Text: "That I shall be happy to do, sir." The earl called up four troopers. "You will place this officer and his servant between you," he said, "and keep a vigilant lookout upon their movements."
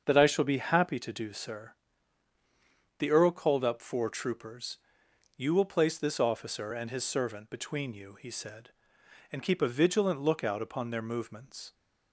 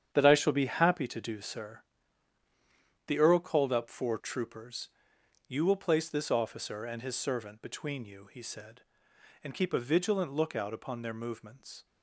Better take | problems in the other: first | gets quieter; strong; throughout; 10 dB // starts louder than the rest; strong; until 1.1 s; 9 dB; also in the first

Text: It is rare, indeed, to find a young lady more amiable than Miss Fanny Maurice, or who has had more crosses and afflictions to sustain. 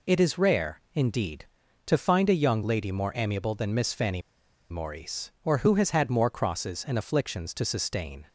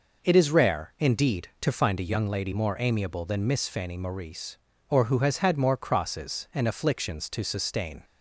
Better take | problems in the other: second | pauses between "Fanny" and "Maurice"; noticeable; at 4.1 s; 0.50 s long

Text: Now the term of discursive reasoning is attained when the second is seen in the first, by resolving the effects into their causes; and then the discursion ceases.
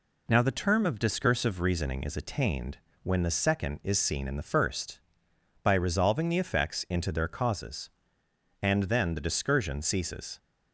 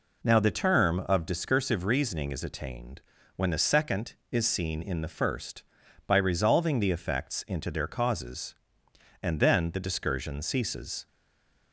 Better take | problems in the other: first | pauses between "attained" and "when"; slight; at 3.0 s; 0.34 s long; slight in the first // stays silent after the last word; slight; from 11.0 s on; 0.7 s long

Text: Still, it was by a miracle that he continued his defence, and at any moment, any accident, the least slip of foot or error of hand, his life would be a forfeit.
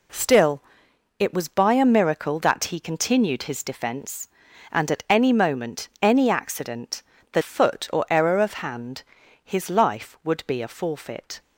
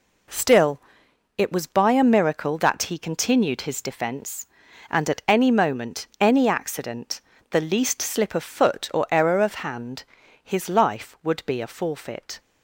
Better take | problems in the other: second | skips "least slip of"; at 7.4 s

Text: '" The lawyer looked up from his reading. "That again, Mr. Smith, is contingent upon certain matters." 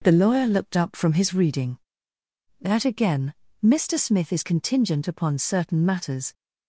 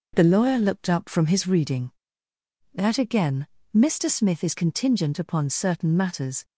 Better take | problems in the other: neither | none

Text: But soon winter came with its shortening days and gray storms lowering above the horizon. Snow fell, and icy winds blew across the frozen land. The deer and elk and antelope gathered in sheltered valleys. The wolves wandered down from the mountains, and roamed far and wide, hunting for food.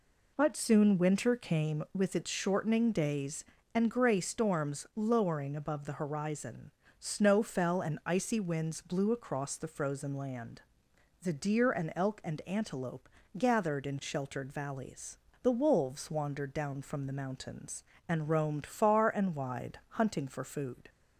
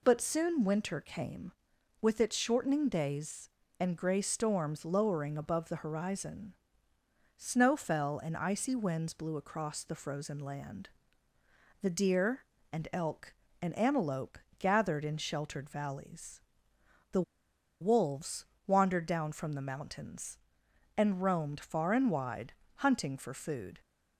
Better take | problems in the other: first | pauses between "antelope" and "gathered"; slight; at 14.3 s; 0.22 s long; slight in the first // pauses between "The" and "wolves"; noticeable; at 17.2 s; 0.58 s long // pauses between "wolves" and "wandered"; slight; at 18.4 s; 0.22 s long

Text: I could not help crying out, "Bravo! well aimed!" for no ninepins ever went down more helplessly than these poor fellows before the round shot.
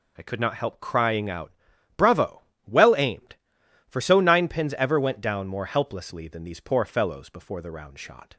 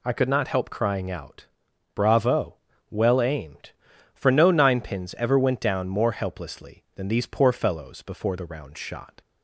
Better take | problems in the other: second | says "so" for "no"; at 4.0 s

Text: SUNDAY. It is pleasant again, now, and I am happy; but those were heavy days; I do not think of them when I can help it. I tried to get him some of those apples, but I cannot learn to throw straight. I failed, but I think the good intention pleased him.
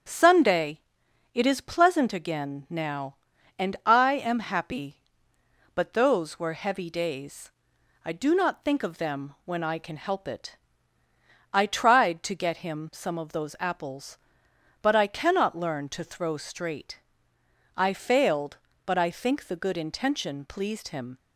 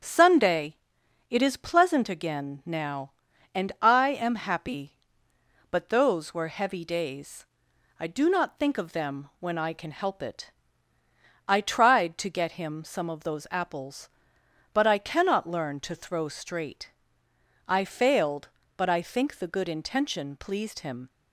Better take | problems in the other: neither | starts louder than the rest; strong; the same in both

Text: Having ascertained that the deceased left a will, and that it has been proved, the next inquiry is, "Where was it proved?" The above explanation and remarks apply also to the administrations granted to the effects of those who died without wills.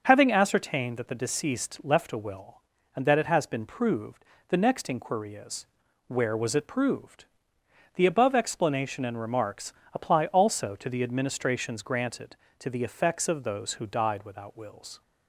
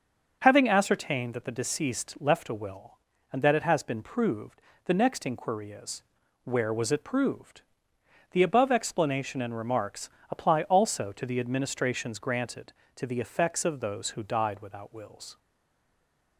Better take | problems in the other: first | starts louder than the rest; until 1.4 s; 6.5 dB; also in the first // pauses between "remarks" and "apply"; slight; at 10.0 s; 0.22 s long; slight in the first // stays silent after the last word; from 15.3 s on; 1.0 s long

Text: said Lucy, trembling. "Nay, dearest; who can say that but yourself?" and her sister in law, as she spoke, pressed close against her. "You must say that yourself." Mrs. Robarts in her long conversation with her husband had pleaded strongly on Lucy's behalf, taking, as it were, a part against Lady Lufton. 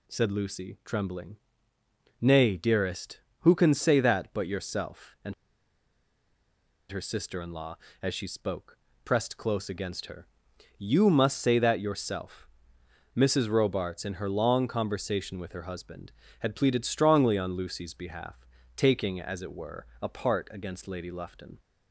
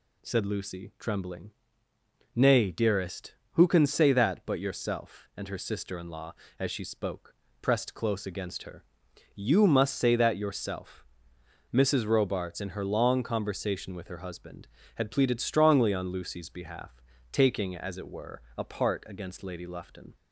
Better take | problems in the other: second | pauses between "and" and "her"; strong; at 5.3 s; 1.5 s long

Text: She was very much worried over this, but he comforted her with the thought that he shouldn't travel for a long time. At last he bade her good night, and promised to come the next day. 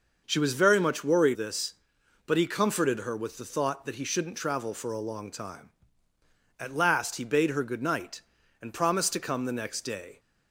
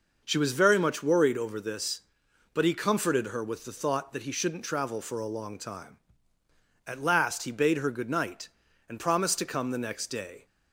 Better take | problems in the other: second | skips "over"; at 1.3 s

